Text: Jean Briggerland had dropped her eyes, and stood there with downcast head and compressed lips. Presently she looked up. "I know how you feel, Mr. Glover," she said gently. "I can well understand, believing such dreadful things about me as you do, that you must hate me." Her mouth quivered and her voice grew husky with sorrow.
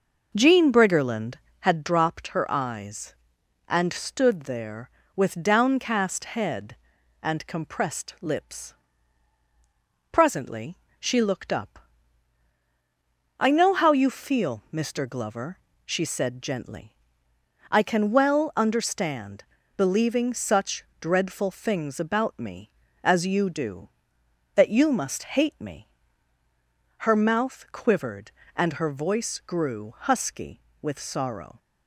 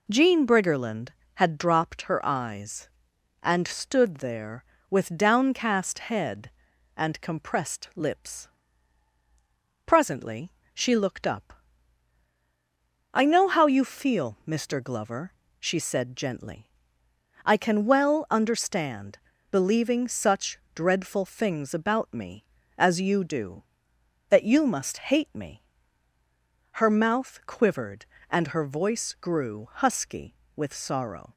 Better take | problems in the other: second | starts louder than the rest; noticeable; until 1.7 s; 5.5 dB // pauses between "Presently" and "she"; slight; at 10.7 s; 0.20 s long; slight in the second // pauses between "such" and "dreadful"; slight; at 20.8 s; 0.18 s long; slight in the second

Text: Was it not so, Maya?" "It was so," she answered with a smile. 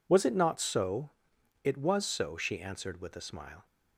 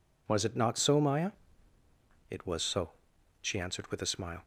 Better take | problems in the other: second | skips "Maya"; at 1.3 s

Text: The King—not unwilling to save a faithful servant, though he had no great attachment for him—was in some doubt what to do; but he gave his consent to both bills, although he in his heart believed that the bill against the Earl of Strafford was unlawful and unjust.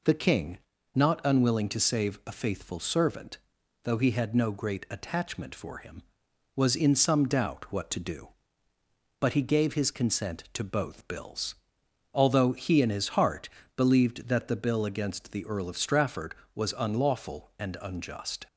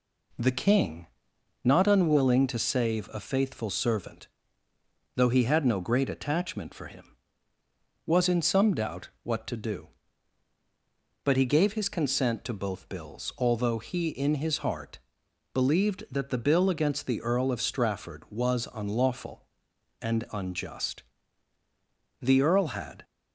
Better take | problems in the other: first | pauses between "heart" and "believed"; noticeable; at 14.9 s; 0.52 s long; slight in the first // goes on to say "The Earl had"; noticeable; from 22.2 s on; 0.82 s long

